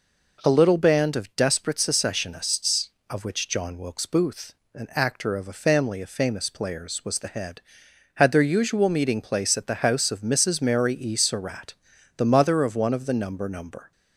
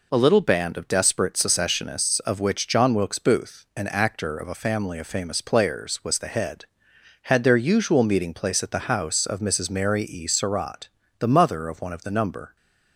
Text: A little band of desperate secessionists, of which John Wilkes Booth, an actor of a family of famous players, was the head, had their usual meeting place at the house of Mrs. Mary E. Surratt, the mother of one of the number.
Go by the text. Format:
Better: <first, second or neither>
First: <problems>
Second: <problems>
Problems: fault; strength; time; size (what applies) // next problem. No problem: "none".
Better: second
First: says "number" twice; at 13.4 s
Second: none